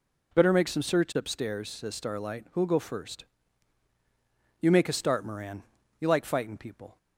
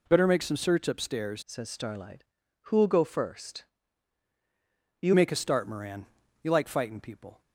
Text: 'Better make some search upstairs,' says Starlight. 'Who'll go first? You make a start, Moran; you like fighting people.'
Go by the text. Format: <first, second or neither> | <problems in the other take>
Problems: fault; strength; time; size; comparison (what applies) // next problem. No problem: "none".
first | changes voice from "says" to "You"; from 1.4 to 5.1 s; 3.7 s long